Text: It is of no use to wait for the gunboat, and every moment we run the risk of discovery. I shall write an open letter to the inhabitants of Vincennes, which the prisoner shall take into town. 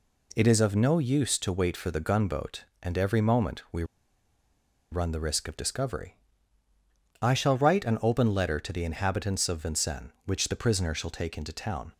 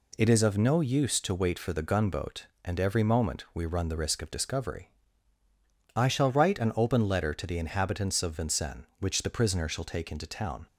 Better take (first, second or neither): second